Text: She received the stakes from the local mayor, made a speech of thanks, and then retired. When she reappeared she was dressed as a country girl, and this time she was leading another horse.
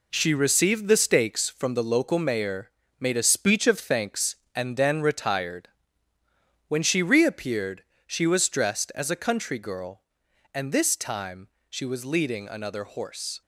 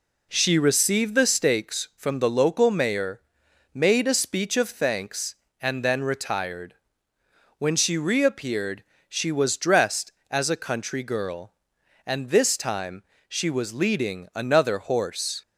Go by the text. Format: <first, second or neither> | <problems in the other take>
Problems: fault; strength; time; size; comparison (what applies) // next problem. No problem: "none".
second | gets quieter; strong; throughout; 8 dB // pauses between "reappeared" and "she"; slight; at 7.8 s; 0.22 s long; slight in the second // pauses between "time" and "she"; slight; at 11.4 s; 0.22 s long; slight in the second